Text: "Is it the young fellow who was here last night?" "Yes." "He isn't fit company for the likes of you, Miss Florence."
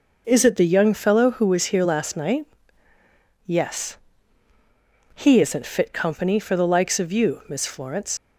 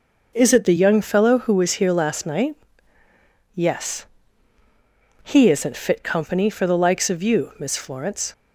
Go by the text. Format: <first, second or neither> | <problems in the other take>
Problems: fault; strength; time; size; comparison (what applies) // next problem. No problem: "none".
second | leaves "Florence" unfinished; at 8.1 s; 45 ms